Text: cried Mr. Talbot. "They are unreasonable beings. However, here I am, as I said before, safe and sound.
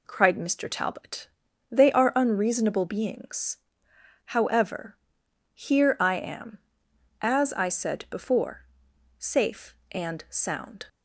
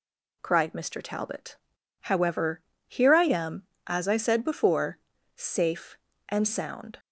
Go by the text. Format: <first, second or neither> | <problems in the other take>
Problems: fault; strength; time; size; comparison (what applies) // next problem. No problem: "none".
first | skips "They are unreasonable beings"; at 1.7 s